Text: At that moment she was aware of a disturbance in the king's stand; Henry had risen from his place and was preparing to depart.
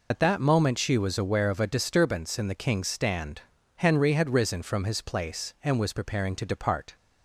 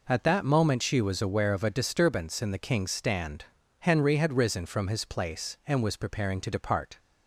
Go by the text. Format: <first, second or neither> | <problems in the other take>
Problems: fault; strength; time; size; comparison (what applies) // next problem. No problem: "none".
second | loses the start of "At"; at 0.1 s; 80 ms